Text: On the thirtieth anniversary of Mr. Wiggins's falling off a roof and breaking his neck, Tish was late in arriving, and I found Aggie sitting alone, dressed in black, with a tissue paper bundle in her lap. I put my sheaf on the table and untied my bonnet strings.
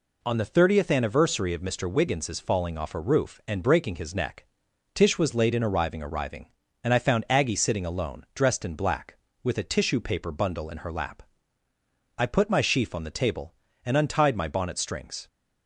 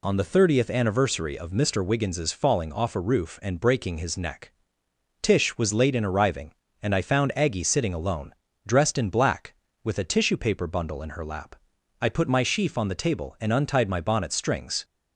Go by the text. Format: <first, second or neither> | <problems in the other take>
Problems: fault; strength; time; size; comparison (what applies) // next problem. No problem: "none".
second | says "arriving" twice; at 6.0 s